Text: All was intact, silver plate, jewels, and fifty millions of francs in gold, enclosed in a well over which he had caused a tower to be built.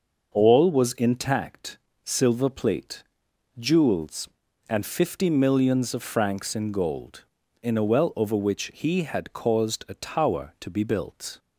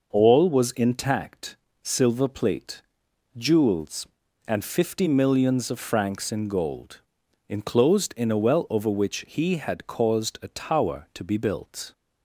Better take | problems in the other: second | starts louder than the rest; noticeable; until 1.3 s; 6 dB // skips "enclosed"; at 7.4 s

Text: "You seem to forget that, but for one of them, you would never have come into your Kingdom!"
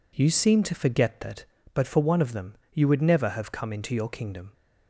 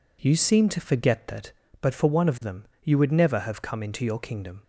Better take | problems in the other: neither | none

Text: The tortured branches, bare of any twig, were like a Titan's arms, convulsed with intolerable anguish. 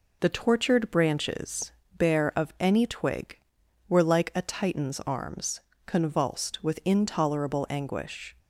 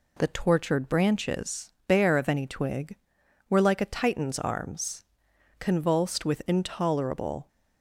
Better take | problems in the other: first | stops before "anguish"; at 7.4 s

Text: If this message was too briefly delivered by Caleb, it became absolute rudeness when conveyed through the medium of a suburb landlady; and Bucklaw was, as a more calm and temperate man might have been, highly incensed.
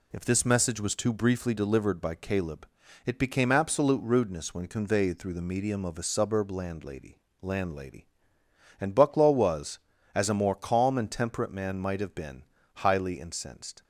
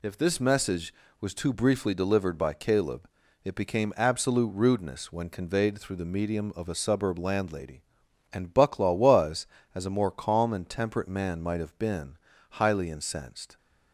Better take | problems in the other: second | says "landlady" twice; at 7.4 s

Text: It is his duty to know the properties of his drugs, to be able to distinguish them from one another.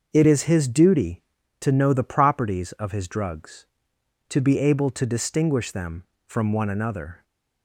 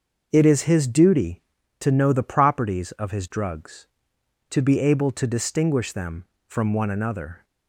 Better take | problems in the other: neither | starts louder than the rest; the same in both

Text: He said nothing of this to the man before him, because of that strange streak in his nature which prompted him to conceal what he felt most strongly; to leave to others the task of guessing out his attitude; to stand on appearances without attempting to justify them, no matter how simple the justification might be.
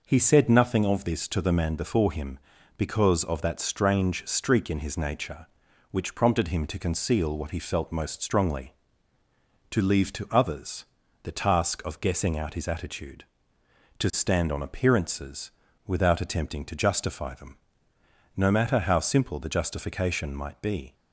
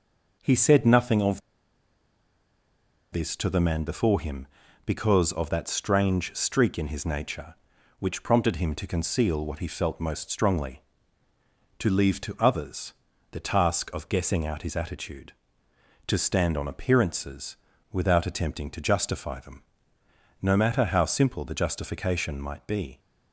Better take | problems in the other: first | pauses between "of" and "this"; strong; at 1.4 s; 1.7 s long // pauses between "others" and "the"; at 12.9 s; 0.38 s long; also in the first // pauses between "appearances" and "without"; at 17.5 s; 0.38 s long; also in the first

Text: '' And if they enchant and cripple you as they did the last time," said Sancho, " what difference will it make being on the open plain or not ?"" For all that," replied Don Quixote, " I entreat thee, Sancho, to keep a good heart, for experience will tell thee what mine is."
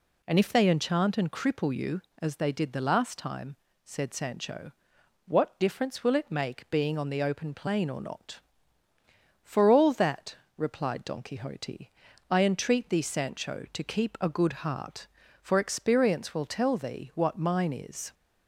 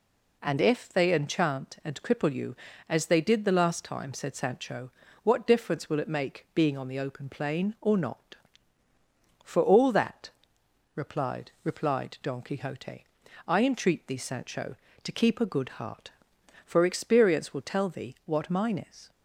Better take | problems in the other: first | says "replied" twice; at 11.6 s

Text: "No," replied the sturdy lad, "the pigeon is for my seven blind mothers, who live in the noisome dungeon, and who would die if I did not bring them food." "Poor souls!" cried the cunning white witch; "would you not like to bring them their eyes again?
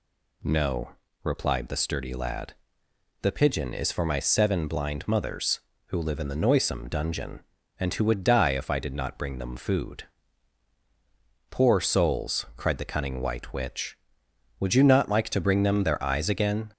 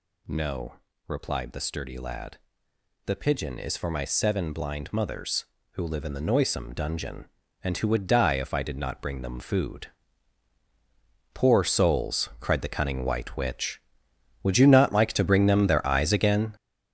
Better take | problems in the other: first | gets louder; strong; throughout; 9 dB

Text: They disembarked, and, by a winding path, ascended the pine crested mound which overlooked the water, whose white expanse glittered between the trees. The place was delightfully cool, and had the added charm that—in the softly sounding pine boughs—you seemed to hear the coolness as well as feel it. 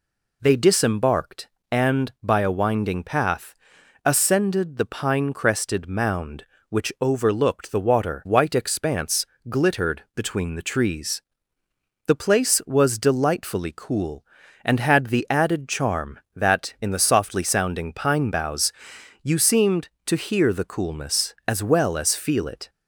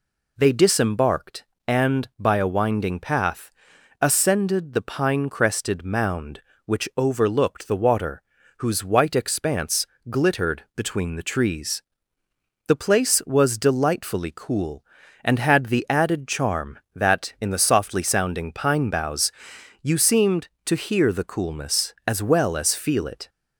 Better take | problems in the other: second | skips "whose"; at 8.2 s // pauses between "expanse" and "glittered"; slight; at 9.2 s; 0.24 s long; slight in the second

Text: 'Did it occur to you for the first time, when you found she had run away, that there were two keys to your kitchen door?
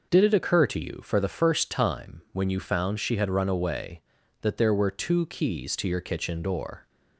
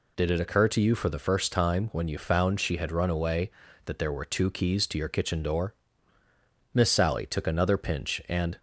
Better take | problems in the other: first | goes on to say "Miss Sally took another pinch and"; strong; from 6.7 s on; 1.8 s long

